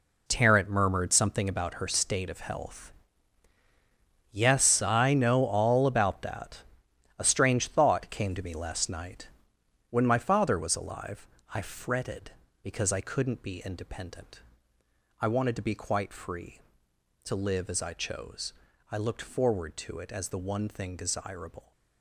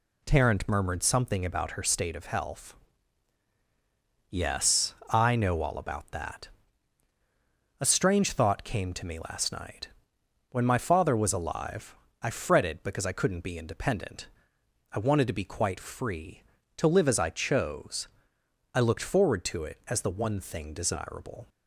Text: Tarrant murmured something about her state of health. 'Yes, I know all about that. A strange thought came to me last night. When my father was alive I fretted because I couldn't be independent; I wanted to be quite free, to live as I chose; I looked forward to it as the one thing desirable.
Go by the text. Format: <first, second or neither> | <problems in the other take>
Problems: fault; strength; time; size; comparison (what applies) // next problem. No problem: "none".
second | gets quieter; strong; throughout; 11.5 dB // pauses between "alive" and "I"; slight; at 11.2 s; 0.26 s long; slight in the second